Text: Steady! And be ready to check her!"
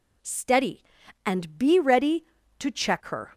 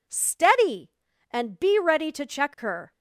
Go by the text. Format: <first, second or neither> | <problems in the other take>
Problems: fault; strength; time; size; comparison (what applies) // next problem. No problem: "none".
neither | none